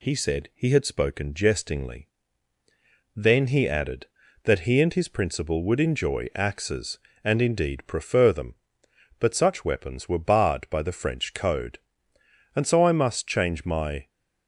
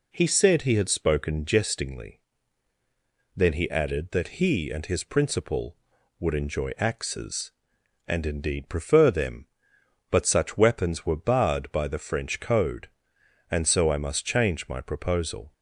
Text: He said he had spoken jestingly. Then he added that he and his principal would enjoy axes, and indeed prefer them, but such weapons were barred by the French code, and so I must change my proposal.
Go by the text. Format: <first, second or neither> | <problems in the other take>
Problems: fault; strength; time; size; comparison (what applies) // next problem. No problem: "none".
second | stops before "proposal"; at 14.0 s